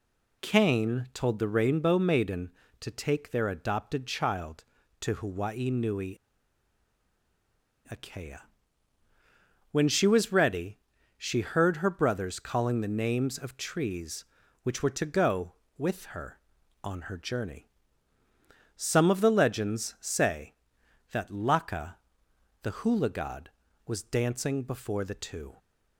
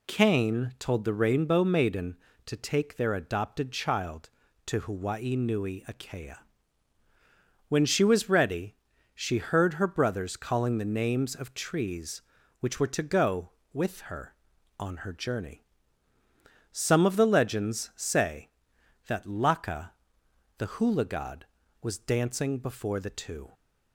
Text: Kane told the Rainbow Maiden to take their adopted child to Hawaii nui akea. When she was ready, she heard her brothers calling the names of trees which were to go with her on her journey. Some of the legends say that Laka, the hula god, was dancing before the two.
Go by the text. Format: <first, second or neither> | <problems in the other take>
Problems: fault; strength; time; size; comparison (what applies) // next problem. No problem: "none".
second | pauses between "nui" and "akea"; strong; at 6.1 s; 1.7 s long